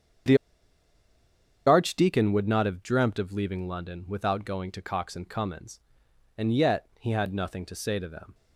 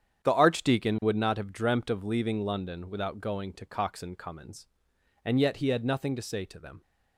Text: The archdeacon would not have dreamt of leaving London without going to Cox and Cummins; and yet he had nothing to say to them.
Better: second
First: starts louder than the rest; strong; until 2.5 s; 8 dB // pauses between "The" and "archdeacon"; strong; at 0.3 s; 1.3 s long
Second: starts louder than the rest; strong; until 1.2 s; 9 dB

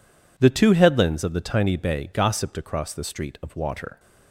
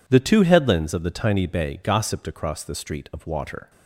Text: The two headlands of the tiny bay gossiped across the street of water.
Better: neither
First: none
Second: none

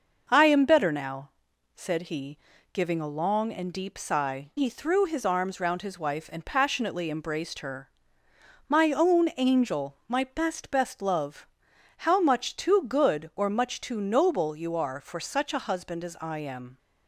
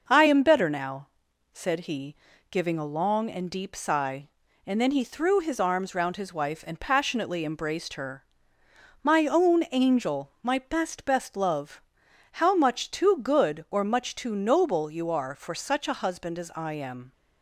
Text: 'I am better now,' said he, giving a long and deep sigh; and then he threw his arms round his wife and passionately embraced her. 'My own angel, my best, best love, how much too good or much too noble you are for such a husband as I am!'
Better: second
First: skips "and then"; at 4.5 s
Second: none

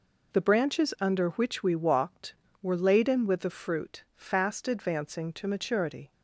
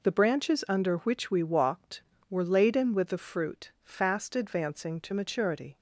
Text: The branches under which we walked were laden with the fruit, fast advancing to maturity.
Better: neither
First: none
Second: none

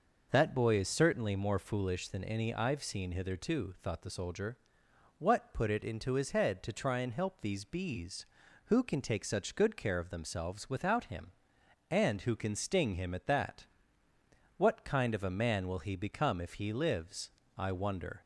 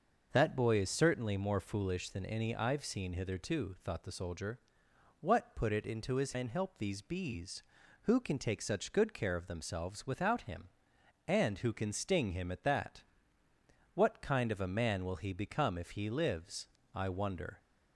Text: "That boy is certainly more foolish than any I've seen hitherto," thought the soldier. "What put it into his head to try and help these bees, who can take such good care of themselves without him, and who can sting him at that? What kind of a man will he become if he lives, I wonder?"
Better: first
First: none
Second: starts louder than the rest; noticeable; until 1.3 s; 6 dB // skips "head to try"; at 6.3 s

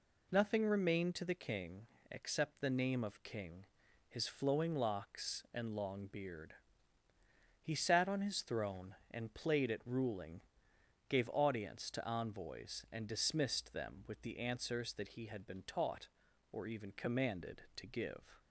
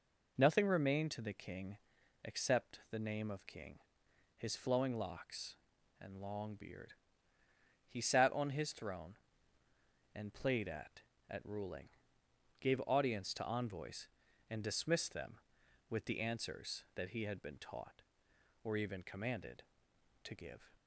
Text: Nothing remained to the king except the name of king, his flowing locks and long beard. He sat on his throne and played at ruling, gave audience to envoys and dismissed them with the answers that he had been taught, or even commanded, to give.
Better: first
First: pauses between "king" and "except"; slight; at 1.8 s; 0.24 s long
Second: pauses between "king" and "except"; noticeable; at 1.7 s; 0.48 s long // says "at" twice; at 11.2 s

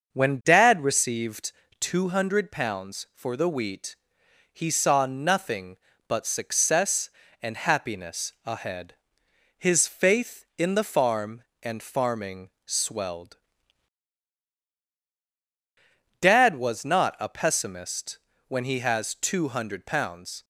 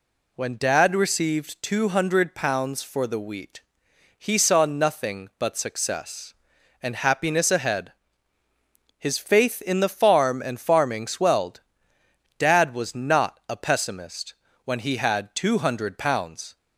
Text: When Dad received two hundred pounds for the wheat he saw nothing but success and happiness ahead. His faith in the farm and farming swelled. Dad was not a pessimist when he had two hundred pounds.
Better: second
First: starts louder than the rest; until 1.1 s; 6.5 dB // pauses between "received" and "two"; slight; at 1.5 s; 0.28 s long // pauses between "wheat" and "he"; noticeable; at 3.9 s; 0.56 s long // pauses between "pessimist" and "when"; slight; at 18.1 s; 0.26 s long // says "has" for "had"; at 18.7 s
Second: pauses between "wheat" and "he"; noticeable; at 3.6 s; 0.56 s long // pauses between "pessimist" and "when"; slight; at 14.3 s; 0.32 s long

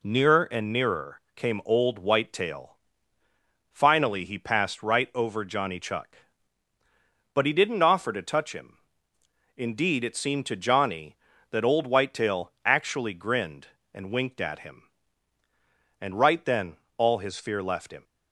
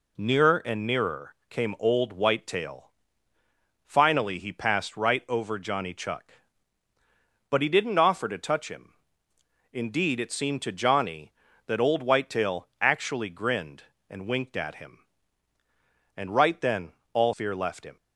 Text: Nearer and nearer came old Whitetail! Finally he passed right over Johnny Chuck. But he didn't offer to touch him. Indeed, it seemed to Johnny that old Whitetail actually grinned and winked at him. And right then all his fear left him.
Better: first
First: pauses between "nearer" and "came"; slight; at 1.1 s; 0.16 s long // pauses between "then" and "all"; slight; at 16.7 s; 0.18 s long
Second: pauses between "nearer" and "came"; slight; at 1.3 s; 0.16 s long // pauses between "then" and "all"; slight; at 16.9 s; 0.18 s long // skips "his"; at 17.3 s

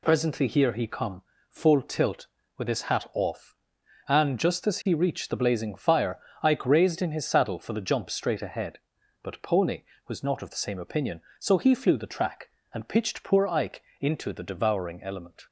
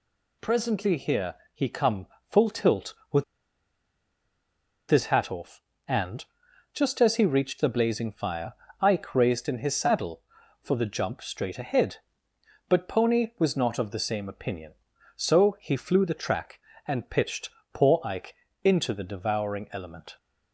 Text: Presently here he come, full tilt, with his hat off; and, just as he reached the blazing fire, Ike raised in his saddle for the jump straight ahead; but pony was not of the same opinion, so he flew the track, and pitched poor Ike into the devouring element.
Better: first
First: pauses between "Ike" and "into"; slight; at 13.8 s; 0.16 s long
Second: pauses between "here" and "he"; slight; at 1.3 s; 0.18 s long // pauses between "with" and "his"; strong; at 3.2 s; 1.6 s long // pauses between "pitched" and "poor"; slight; at 17.5 s; 0.22 s long // pauses between "Ike" and "into"; slight; at 18.3 s; 0.30 s long

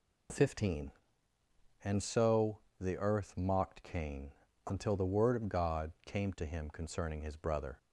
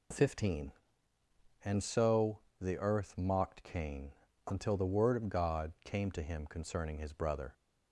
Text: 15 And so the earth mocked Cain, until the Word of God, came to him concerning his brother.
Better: neither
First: pauses between "so" and "the"; slight; at 2.5 s; 0.20 s long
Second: pauses between "so" and "the"; slight; at 2.3 s; 0.20 s long

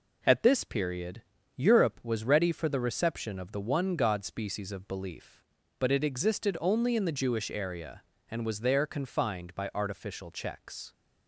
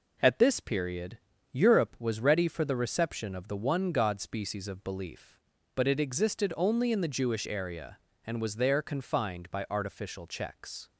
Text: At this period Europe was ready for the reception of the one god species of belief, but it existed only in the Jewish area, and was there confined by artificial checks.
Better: neither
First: pauses between "period" and "Europe"; slight; at 1.2 s; 0.34 s long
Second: pauses between "period" and "Europe"; slight; at 1.1 s; 0.34 s long

